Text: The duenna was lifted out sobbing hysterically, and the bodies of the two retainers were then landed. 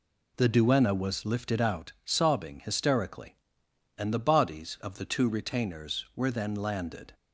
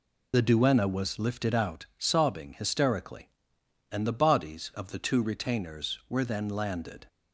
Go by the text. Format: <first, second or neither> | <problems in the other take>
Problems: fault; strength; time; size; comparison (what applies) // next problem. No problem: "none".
first | loses the start of "The"; at 0.3 s; 40 ms